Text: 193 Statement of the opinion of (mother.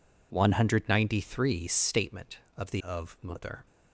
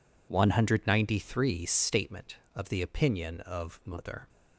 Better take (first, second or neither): second